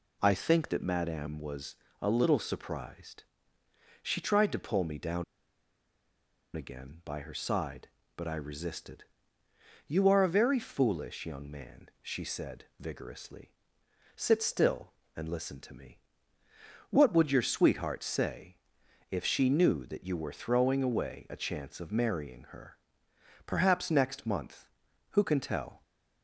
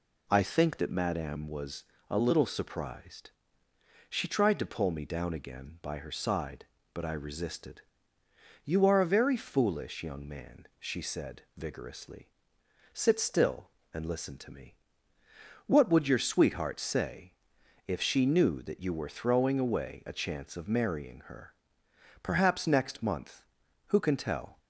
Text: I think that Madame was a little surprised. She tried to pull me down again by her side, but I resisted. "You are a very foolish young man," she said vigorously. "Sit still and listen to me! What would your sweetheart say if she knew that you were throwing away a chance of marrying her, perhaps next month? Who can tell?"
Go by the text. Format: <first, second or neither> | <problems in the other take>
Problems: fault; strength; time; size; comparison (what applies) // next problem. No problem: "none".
second | pauses between "was" and "a"; slight; at 1.7 s; 0.24 s long; slight in the second // pauses between "down" and "again"; strong; at 5.2 s; 1.3 s long // pauses between "say" and "if"; noticeable; at 18.5 s; 0.54 s long; noticeable in the second